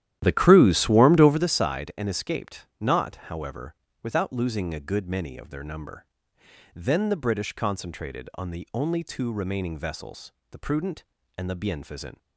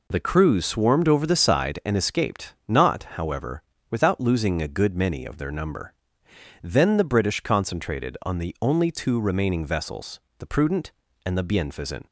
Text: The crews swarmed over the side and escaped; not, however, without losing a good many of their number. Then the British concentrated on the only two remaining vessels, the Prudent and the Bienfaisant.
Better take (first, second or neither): second